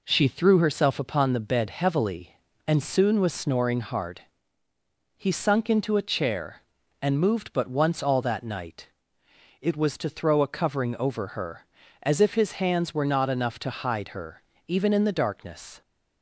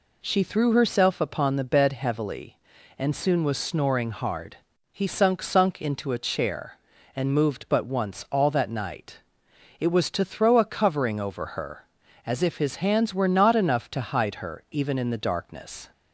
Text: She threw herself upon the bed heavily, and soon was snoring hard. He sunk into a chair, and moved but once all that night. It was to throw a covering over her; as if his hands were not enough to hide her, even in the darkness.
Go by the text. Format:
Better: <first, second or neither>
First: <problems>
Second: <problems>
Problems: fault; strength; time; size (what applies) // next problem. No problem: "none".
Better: first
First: none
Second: says "sunk" twice; at 5.4 s